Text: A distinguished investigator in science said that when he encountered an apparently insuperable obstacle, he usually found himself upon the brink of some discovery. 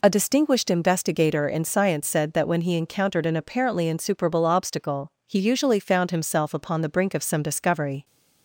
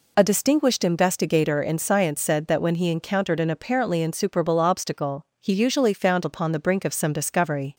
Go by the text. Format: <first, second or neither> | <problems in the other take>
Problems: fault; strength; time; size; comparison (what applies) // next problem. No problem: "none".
first | skips "himself"; at 6.2 s